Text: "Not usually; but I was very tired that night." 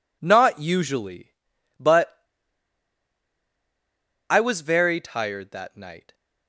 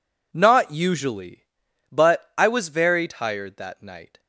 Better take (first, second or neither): second